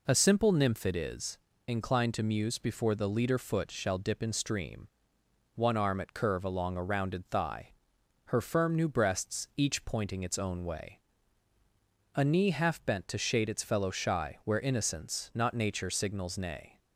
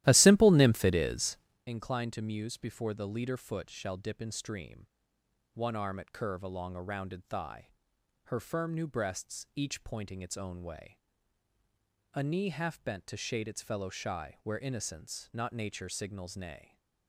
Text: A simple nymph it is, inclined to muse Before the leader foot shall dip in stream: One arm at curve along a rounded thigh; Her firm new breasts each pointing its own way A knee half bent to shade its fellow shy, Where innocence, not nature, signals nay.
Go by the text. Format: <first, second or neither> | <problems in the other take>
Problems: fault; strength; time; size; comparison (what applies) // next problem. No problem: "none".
first | starts louder than the rest; strong; until 1.7 s; 14.5 dB // pauses between "way" and "A"; at 10.9 s; 1.1 s long; also in the first